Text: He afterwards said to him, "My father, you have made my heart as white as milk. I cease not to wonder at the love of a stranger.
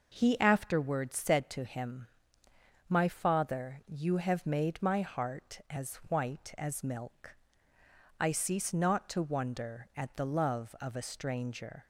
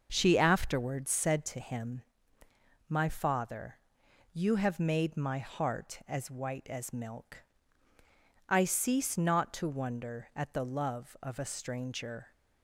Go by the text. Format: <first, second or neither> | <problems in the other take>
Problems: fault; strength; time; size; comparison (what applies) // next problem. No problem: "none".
first | starts louder than the rest; noticeable; until 1.1 s; 6 dB // says "She" for "He"; at 0.1 s